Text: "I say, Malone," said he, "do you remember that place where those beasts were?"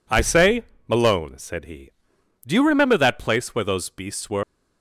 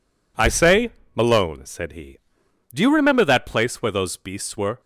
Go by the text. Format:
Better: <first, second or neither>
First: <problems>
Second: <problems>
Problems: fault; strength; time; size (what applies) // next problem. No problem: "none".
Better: second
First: leaves "were" unfinished; at 4.4 s; 100 ms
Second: none